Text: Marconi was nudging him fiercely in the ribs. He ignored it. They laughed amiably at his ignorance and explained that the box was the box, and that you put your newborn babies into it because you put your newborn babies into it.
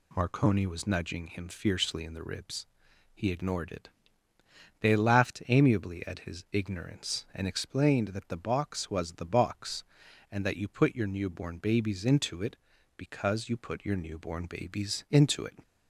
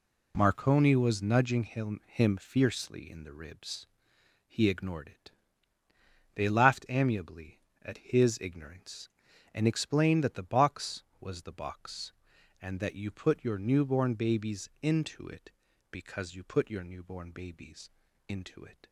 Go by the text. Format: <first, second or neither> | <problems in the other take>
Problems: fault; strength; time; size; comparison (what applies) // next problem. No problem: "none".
first | says "him" twice; at 2.0 s // pauses between "babies" and "into"; at 17.8 s; 0.40 s long